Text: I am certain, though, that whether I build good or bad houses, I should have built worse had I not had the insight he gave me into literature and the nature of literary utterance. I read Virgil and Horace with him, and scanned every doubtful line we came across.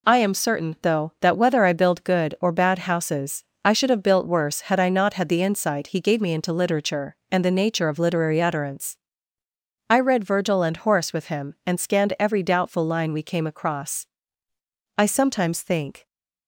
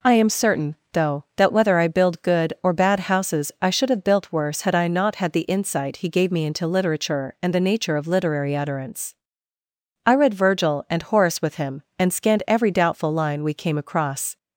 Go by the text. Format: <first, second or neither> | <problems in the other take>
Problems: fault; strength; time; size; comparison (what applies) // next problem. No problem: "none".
second | goes on to say "I sometimes think"; noticeable; from 14.9 s on; 1.0 s long